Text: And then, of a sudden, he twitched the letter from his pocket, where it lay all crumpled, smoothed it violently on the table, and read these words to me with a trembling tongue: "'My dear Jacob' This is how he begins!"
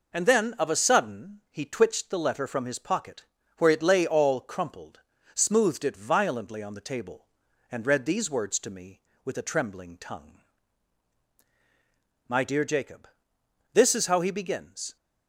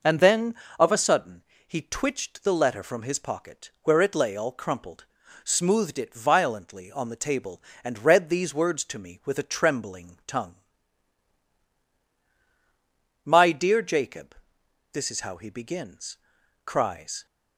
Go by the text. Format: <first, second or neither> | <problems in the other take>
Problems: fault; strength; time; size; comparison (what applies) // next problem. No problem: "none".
first | pauses between "Jacob" and "This"; noticeable; at 14.3 s; 0.58 s long; noticeable in the first // goes on to say "cries"; from 16.6 s on; 0.60 s long